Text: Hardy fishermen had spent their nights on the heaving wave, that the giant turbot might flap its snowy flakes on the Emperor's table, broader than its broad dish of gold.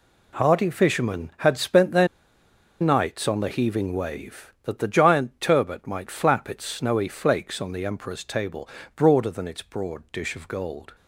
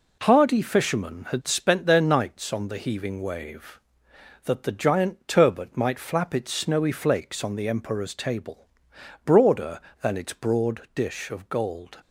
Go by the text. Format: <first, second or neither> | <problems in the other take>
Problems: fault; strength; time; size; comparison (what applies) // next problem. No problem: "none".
second | pauses between "their" and "nights"; noticeable; at 2.0 s; 0.73 s long